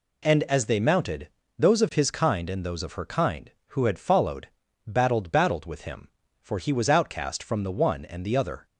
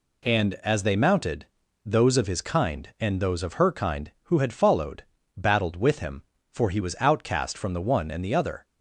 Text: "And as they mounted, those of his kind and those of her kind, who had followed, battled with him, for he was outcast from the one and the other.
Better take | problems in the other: second | says "battled" twice; at 5.2 s

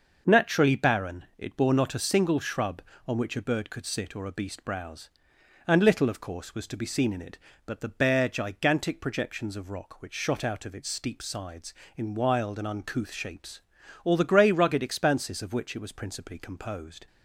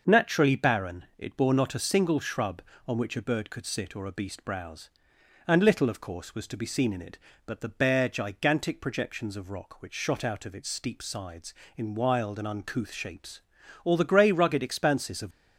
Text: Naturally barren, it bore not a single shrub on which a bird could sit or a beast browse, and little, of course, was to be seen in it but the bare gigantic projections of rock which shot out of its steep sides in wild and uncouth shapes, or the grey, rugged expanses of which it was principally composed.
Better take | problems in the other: first | starts louder than the rest; noticeable; until 1.2 s; 6 dB; noticeable in the first // stops before "which it was principally composed"; at 15.3 s

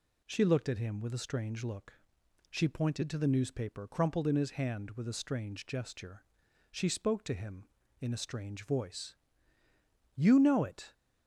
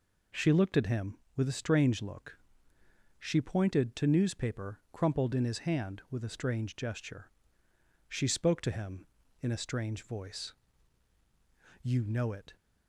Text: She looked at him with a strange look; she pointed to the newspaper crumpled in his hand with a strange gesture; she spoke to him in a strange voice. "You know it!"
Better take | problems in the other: first | skips "the"; at 4.0 s

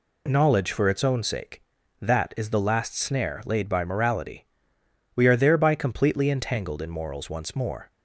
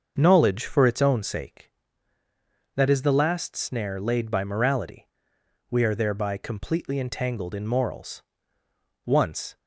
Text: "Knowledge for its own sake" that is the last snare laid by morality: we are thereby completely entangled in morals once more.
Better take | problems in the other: first | starts louder than the rest; until 1.1 s; 6 dB // pauses between "morals" and "once"; noticeable; at 8.2 s; 0.82 s long // stops before "more"; at 9.5 s

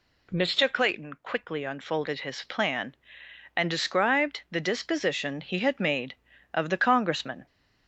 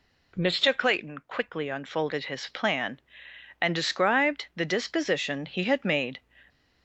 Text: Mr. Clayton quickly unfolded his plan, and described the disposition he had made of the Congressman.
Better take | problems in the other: first | stops before "of the Congressman"; at 6.4 s

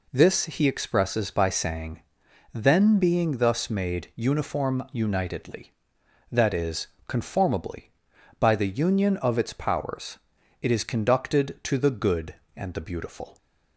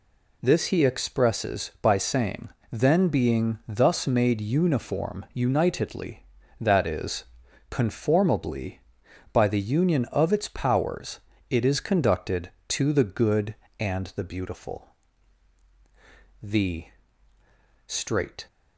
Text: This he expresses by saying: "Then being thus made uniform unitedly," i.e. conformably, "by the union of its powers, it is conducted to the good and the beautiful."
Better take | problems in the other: first | goes on to say "The straight"; strong; from 16.3 s on; 2.0 s long

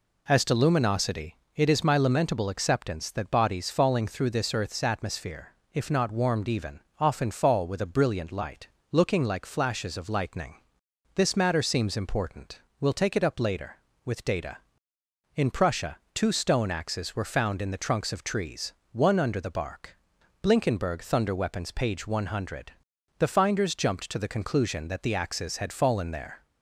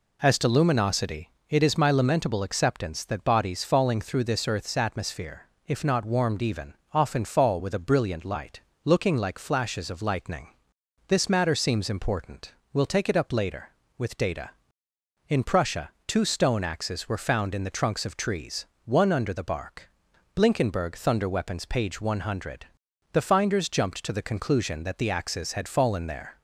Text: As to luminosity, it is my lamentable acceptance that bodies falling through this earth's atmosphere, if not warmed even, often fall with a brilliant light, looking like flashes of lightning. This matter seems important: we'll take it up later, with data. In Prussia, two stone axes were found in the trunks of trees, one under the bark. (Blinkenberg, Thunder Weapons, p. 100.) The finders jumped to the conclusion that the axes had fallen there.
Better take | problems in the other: neither | none

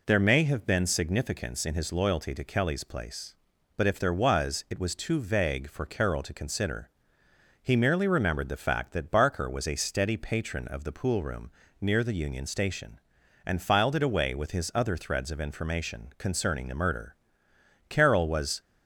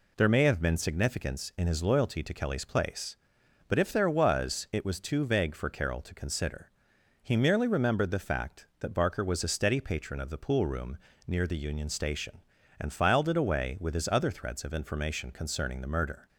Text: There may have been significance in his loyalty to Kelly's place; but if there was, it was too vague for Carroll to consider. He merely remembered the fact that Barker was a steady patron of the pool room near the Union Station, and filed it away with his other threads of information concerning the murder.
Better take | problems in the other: second | pauses between "room" and "near"; slight; at 11.5 s; 0.30 s long; slight in the second // goes on to say "Carroll was"; noticeable; from 17.8 s on; 0.72 s long

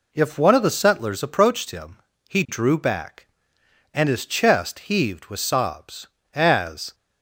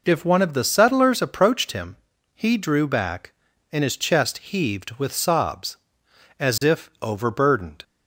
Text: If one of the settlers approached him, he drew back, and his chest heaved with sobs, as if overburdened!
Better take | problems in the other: second | stops before "if overburdened"; at 6.9 s

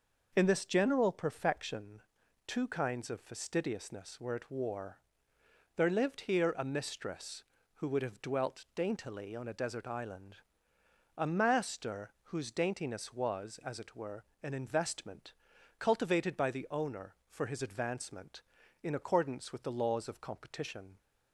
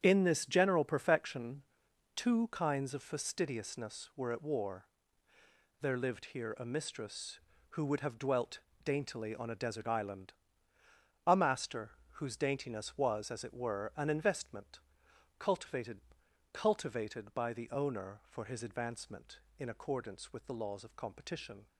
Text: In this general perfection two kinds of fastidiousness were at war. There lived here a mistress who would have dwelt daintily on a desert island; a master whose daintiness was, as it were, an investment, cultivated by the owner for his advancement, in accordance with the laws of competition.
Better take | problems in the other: first | starts louder than the rest; strong; until 1.0 s; 8.5 dB // pauses between "perfection" and "two"; noticeable; at 1.6 s; 0.54 s long; noticeable in the first // pauses between "dwelt" and "daintily"; slight; at 8.6 s; 0.22 s long // pauses between "master" and "whose"; slight; at 11.9 s; 0.22 s long // says "cultivated" twice; at 16.5 s

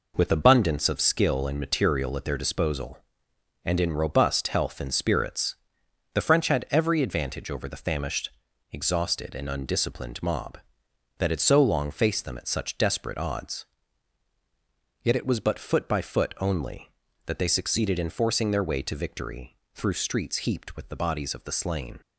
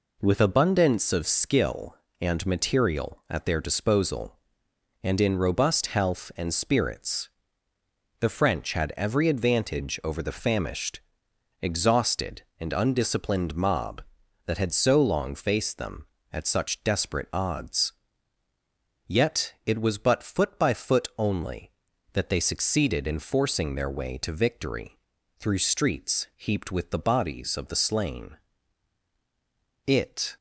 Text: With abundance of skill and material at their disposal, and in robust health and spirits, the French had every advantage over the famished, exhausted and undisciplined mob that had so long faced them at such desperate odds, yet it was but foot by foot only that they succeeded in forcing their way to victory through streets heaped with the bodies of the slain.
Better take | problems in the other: first | pauses between "victory" and "through"; at 24.9 s; 0.44 s long; slight in the first // goes on to say "It"; from 29.8 s on; 0.50 s long

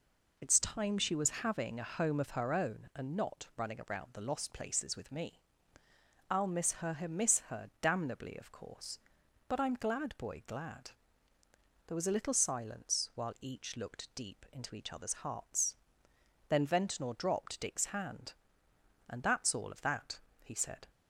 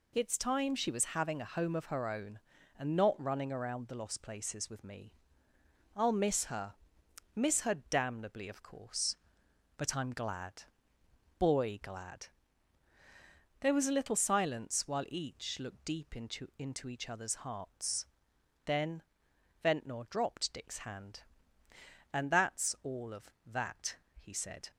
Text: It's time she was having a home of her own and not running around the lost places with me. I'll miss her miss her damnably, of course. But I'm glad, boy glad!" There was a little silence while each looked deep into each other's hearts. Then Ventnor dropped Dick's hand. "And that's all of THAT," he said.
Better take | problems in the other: first | pauses between "her" and "miss"; noticeable; at 6.7 s; 0.60 s long // pauses between "her" and "damnably"; slight; at 7.7 s; 0.16 s long // says "into" twice; at 16.6 s // pauses between "Then" and "Ventnor"; noticeable; at 19.0 s; 0.62 s long

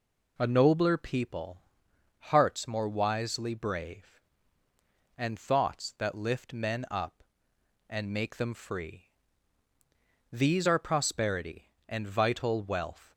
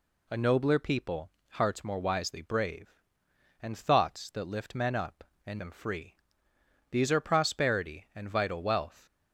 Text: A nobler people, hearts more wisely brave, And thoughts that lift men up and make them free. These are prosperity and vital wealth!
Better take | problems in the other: first | skips "make"; at 5.5 s

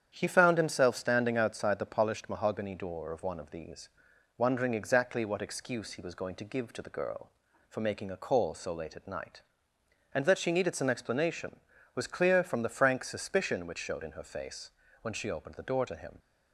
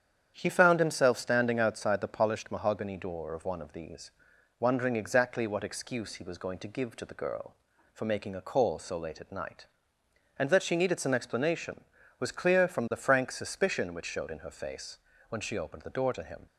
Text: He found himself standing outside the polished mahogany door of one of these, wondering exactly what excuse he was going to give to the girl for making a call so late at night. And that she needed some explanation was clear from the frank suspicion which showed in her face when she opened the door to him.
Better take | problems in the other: neither | starts louder than the rest; strong; the same in both // pauses between "face" and "when"; slight; the same in both

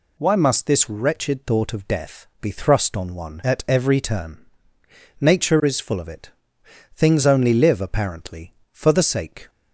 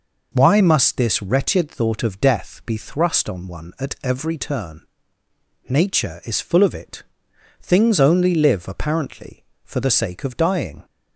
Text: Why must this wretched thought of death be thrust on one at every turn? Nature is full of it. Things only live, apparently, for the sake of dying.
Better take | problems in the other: second | pauses between "death" and "be"; slight; at 2.2 s; 0.16 s long // stops before "of dying"; at 9.4 s

